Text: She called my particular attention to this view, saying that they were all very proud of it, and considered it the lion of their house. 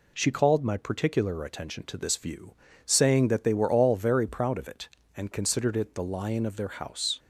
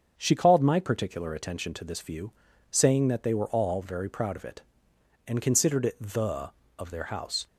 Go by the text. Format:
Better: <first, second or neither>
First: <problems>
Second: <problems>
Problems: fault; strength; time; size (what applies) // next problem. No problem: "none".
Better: first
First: none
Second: starts louder than the rest; until 1.1 s; 7 dB // skips "lion"; at 6.6 s